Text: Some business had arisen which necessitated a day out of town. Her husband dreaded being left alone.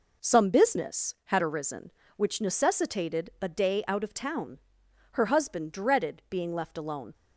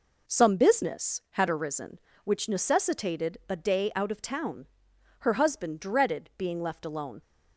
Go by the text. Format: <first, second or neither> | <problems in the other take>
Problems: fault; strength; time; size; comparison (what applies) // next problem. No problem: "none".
neither | none